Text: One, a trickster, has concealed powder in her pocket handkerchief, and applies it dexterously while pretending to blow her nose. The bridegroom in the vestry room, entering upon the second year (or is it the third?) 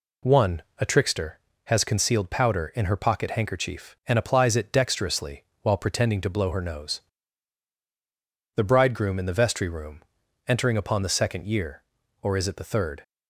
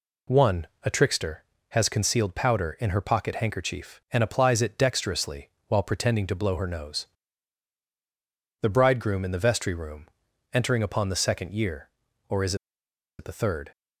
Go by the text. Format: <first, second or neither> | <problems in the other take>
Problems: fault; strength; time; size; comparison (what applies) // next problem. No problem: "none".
first | pauses between "dexterously" and "while"; slight; at 5.4 s; 0.20 s long; slight in the first // pauses between "is" and "it"; noticeable; at 12.5 s; 0.64 s long